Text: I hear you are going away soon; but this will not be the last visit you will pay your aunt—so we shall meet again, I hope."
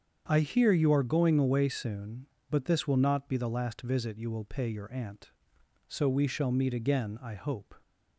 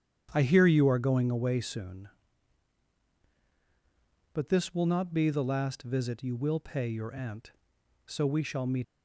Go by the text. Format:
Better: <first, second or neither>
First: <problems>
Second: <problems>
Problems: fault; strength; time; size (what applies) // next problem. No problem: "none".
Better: first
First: starts louder than the rest; strong; until 1.2 s; 7.5 dB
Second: starts louder than the rest; strong; until 1.3 s; 9 dB // stops before "again I hope"; at 8.8 s